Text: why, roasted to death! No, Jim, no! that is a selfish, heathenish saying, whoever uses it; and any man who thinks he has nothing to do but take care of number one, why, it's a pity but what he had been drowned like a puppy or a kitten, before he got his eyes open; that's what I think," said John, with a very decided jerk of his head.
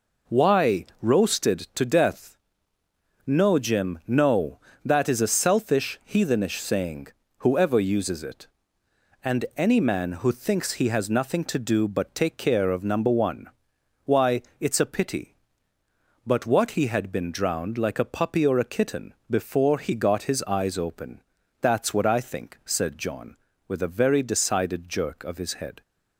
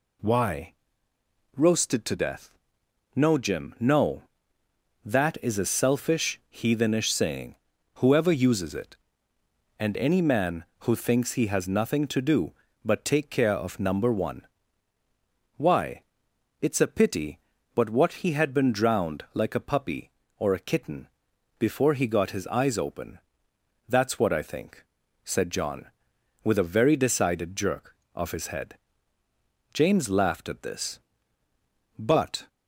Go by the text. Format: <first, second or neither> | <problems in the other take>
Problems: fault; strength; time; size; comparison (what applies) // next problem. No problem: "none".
first | goes on to say "James laughed at this but"; strong; from 29.7 s on; 2.7 s long